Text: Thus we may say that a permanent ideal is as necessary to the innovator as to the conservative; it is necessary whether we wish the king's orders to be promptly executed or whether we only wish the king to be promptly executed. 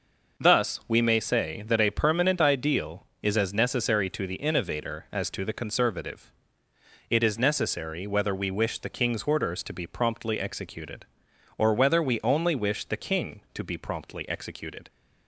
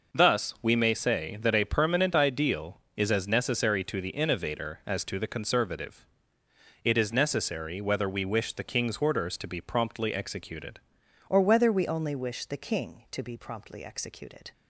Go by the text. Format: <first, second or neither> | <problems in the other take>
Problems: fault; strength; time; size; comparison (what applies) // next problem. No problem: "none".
first | changes voice at "or"; from 11.2 s on; 3.3 s long